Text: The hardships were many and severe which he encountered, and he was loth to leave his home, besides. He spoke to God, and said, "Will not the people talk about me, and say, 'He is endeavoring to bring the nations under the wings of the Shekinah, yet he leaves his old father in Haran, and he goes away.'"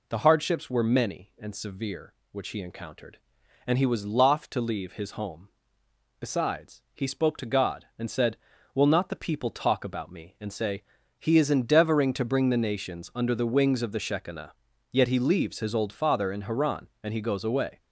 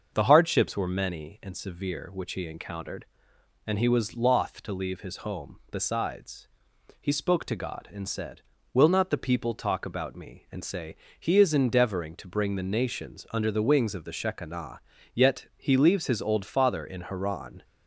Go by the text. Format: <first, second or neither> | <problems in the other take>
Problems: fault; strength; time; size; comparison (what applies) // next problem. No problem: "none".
first | starts louder than the rest; until 1.1 s; 6.5 dB // stops before "and he goes away"; at 17.6 s